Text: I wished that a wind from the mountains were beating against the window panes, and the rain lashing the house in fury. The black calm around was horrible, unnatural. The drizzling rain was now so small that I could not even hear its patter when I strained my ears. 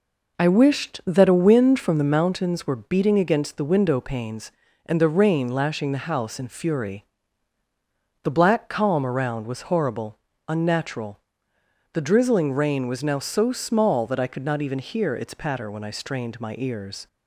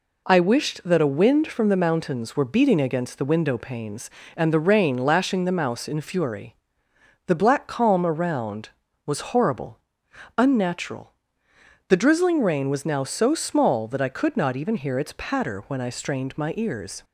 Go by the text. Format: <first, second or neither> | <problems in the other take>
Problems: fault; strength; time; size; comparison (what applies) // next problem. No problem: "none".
first | says "mouse" for "house"; at 5.5 s